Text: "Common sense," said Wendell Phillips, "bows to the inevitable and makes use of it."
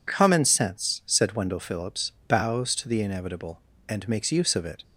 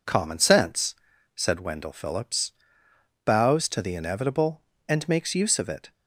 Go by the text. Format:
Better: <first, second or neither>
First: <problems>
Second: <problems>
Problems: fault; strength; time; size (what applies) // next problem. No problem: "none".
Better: neither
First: none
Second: none